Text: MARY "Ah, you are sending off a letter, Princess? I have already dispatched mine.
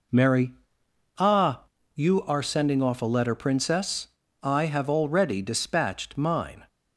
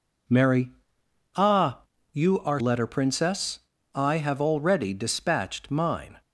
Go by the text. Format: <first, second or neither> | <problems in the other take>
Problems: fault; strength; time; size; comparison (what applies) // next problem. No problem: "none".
first | pauses between "MARY" and "Ah"; noticeable; at 0.7 s; 0.66 s long; noticeable in the first // skips "sending off a"; at 2.6 s